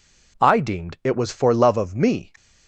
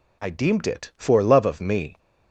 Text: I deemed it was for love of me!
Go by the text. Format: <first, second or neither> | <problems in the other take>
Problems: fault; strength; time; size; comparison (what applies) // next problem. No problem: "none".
first | skips "was"; at 0.9 s